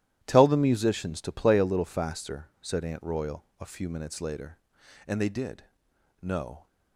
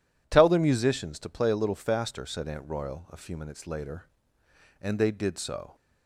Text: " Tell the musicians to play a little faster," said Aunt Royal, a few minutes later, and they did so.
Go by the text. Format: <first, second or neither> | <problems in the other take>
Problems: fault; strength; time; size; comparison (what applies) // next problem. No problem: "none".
second | starts louder than the rest; strong; until 1.2 s; 13 dB // says "no" for "so"; at 6.2 s